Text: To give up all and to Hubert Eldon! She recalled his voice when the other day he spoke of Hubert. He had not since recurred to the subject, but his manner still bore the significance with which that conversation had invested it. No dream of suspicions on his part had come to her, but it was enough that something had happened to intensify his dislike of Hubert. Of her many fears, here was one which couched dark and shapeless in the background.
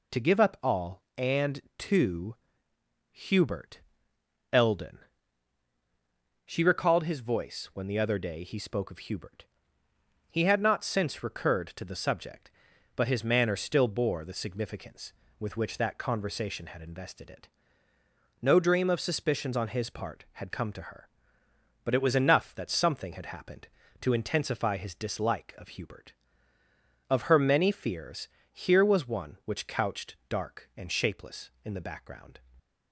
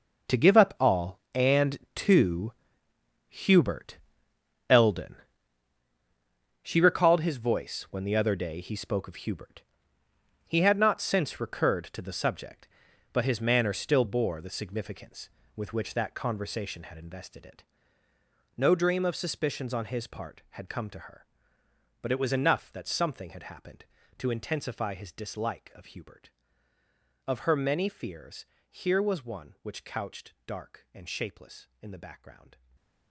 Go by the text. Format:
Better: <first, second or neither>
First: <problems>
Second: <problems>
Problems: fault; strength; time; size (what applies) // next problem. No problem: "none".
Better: first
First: pauses between "to" and "Hubert"; noticeable; at 2.3 s; 0.76 s long // pauses between "Hubert" and "Eldon"; noticeable; at 3.8 s; 0.72 s long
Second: gets quieter; strong; throughout; 14.5 dB // pauses between "to" and "Hubert"; noticeable; at 2.5 s; 0.76 s long // pauses between "Hubert" and "Eldon"; noticeable; at 3.9 s; 0.72 s long // stays silent after the last word; slight; from 32.5 s on; 0.5 s long